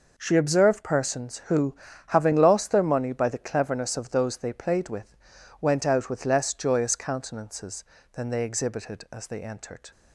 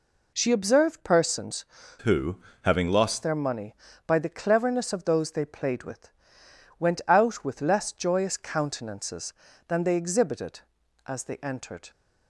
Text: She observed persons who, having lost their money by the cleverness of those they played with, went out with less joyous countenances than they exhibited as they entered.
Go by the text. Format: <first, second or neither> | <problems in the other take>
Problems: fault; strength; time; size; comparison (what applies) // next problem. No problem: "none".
first | changes voice from "who" to "lost"; from 1.9 to 3.2 s; 1.3 s long